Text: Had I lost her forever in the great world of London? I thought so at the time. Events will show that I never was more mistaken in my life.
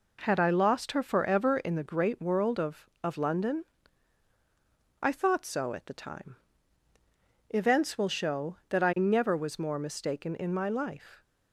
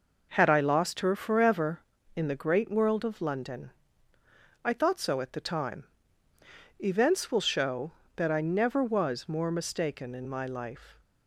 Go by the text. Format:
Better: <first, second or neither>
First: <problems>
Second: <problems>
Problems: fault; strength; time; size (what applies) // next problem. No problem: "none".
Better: second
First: says "of" twice; at 3.0 s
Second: none